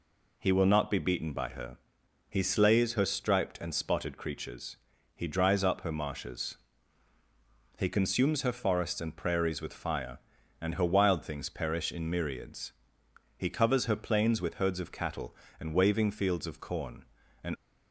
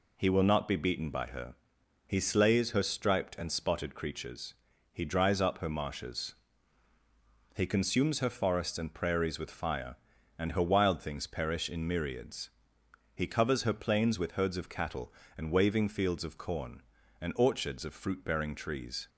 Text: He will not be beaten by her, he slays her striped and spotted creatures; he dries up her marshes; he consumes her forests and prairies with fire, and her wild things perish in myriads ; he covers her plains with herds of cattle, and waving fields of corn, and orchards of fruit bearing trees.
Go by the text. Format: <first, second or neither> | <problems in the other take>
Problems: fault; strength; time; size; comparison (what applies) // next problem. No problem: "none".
second | stops before "orchards of fruit bearing trees"; at 17.5 s